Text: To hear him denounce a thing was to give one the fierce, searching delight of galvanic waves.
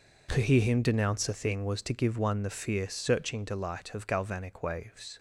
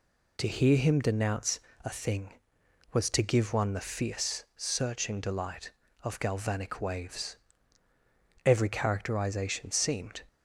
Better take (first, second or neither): first